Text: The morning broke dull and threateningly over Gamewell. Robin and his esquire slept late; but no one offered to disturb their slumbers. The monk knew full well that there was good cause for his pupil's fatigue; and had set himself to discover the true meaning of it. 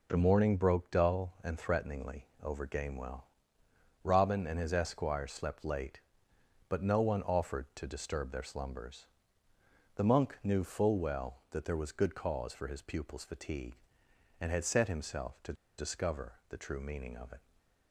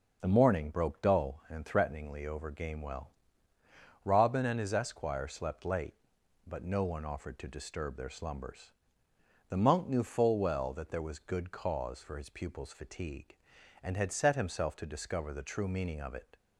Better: second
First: pauses between "threateningly" and "over"; slight; at 2.2 s; 0.16 s long // pauses between "to" and "discover"; slight; at 15.5 s; 0.25 s long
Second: none

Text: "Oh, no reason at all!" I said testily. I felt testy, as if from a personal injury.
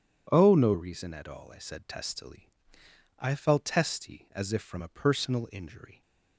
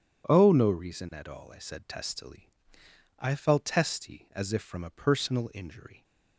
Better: neither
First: none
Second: none

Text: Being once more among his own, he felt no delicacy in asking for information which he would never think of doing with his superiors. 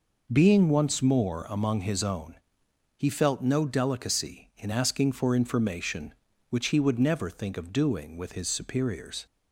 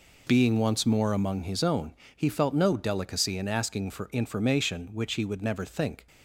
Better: first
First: none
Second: stops before "of doing with his superiors"; at 6.0 s

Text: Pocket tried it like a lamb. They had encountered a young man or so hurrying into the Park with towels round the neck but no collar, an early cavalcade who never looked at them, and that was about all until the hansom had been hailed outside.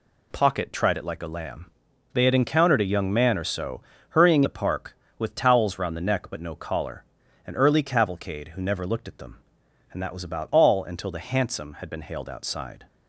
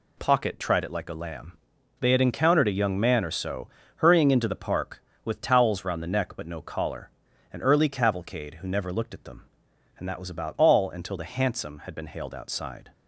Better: second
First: pauses between "so" and "hurrying"; slight; at 3.8 s; 0.28 s long // skips "into"; at 4.4 s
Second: pauses between "so" and "hurrying"; slight; at 3.6 s; 0.28 s long

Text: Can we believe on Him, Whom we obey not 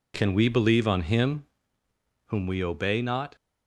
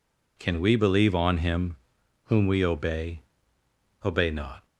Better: first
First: none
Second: says "obey" twice; at 4.0 s

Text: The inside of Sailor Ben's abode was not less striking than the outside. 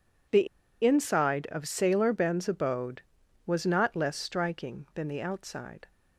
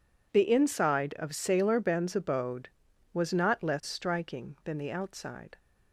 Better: second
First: pauses between "The" and "inside"; at 0.4 s; 0.36 s long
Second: none

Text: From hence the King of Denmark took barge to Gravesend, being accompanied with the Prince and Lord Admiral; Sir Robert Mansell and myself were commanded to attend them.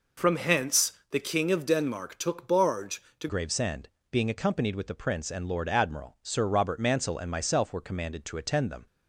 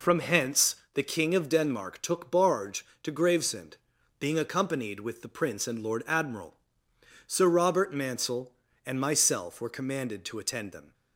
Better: second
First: pauses between "hence" and "the"; slight; at 0.9 s; 0.22 s long // changes voice at "Gravesend"; from 3.2 s on; 5.6 s long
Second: pauses between "hence" and "the"; slight; at 0.7 s; 0.22 s long

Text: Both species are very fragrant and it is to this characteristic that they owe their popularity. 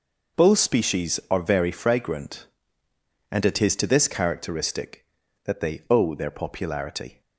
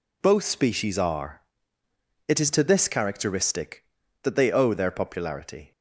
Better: first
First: none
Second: skips "very fragrant and"; at 1.8 s

